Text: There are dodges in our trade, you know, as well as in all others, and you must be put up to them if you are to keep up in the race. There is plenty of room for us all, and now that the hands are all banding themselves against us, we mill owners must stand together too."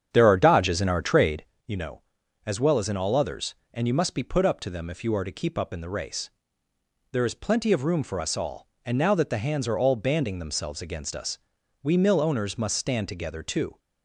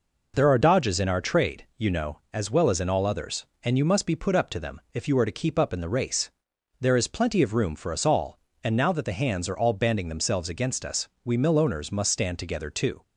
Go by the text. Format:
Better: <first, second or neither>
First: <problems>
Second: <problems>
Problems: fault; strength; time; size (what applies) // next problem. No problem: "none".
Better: second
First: starts louder than the rest; strong; until 1.6 s; 8 dB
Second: none